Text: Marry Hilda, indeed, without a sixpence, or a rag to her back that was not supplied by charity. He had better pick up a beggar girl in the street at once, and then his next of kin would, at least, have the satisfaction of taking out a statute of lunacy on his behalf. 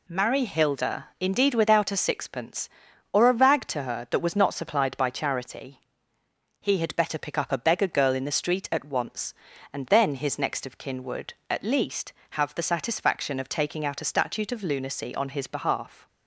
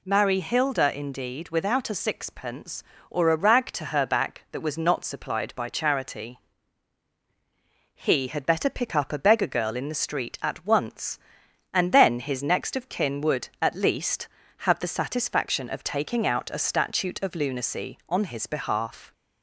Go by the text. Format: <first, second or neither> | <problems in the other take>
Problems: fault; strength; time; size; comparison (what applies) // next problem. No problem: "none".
second | skips "back"; at 4.0 s